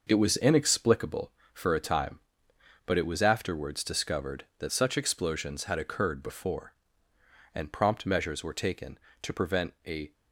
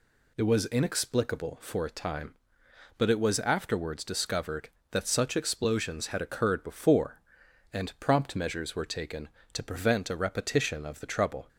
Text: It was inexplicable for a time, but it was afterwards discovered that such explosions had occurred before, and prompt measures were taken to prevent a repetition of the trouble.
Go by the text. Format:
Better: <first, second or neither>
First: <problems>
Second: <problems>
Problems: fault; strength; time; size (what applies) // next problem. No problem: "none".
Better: second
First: stops before "repetition of the trouble"; at 10.1 s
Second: none